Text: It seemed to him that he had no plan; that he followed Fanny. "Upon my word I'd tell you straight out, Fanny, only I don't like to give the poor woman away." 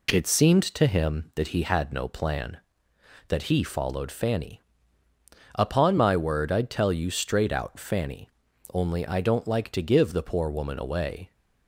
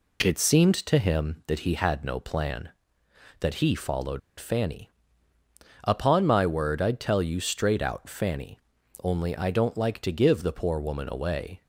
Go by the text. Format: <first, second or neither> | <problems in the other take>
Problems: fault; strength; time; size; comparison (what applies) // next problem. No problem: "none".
first | pauses between "followed" and "Fanny"; slight; at 4.2 s; 0.18 s long